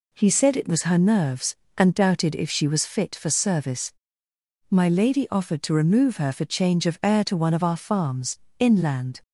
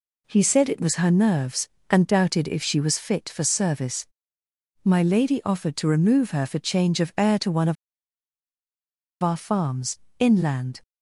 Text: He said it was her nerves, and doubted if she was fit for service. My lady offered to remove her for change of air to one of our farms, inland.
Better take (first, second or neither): first